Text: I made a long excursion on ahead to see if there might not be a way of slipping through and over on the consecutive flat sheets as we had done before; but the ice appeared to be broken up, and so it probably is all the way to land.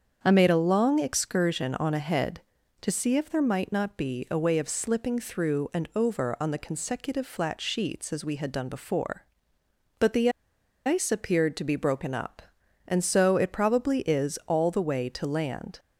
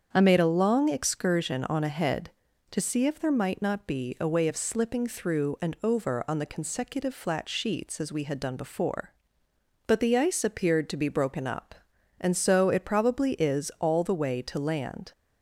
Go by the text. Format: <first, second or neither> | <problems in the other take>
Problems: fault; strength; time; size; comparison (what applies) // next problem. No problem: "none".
second | starts louder than the rest; strong; until 1.2 s; 7.5 dB; strong in the second // pauses between "the" and "ice"; noticeable; at 10.2 s; 0.57 s long